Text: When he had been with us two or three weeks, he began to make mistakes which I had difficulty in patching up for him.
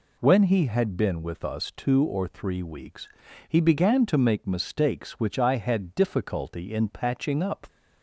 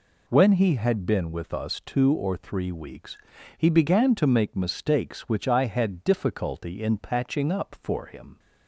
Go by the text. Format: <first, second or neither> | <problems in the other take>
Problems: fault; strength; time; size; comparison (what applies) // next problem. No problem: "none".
second | stops before "for him"; at 7.6 s